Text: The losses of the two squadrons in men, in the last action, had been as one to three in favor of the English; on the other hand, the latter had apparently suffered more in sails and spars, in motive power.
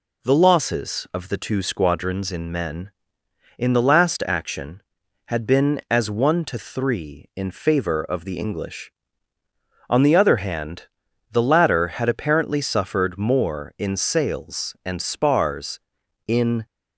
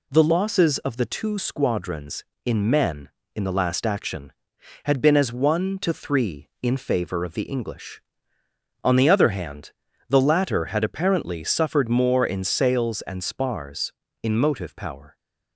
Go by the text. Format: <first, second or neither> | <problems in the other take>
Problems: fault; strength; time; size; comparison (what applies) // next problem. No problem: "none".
second | stops before "motive power"; at 16.6 s